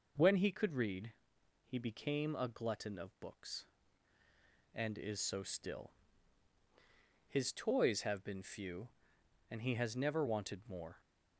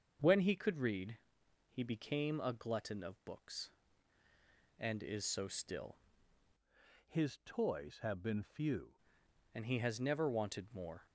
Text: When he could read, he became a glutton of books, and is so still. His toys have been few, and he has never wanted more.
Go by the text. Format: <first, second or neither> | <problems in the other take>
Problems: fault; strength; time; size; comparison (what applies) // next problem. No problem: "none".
first | starts louder than the rest; until 1.7 s; 6.5 dB // changes voice from "His" to "few"; from 7.0 to 8.9 s; 1.9 s long